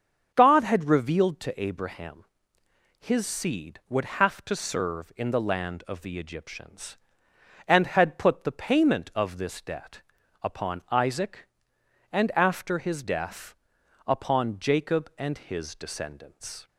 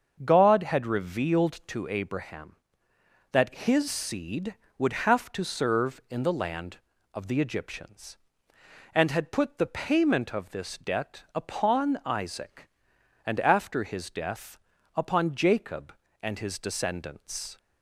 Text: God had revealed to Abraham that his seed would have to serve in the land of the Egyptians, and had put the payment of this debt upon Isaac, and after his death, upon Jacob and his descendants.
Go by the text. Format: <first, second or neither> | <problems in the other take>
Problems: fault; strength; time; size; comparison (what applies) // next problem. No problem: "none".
second | starts louder than the rest; until 1.3 s; 7 dB; also in the second // skips "that"; at 2.6 s // pauses between "debt" and "upon"; at 10.0 s; 0.40 s long